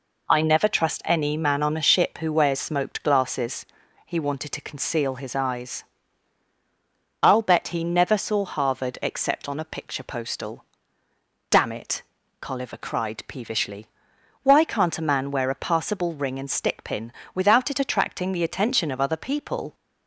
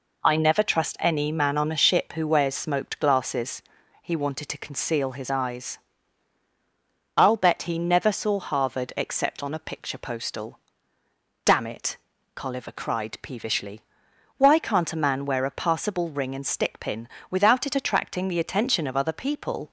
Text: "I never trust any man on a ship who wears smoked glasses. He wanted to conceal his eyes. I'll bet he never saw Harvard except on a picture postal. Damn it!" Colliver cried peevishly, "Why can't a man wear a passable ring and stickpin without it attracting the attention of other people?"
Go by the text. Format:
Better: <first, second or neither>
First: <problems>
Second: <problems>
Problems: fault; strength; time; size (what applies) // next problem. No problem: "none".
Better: neither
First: pauses between "stickpin" and "without"; slight; at 17.1 s; 0.22 s long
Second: pauses between "stickpin" and "without"; slight; at 17.0 s; 0.22 s long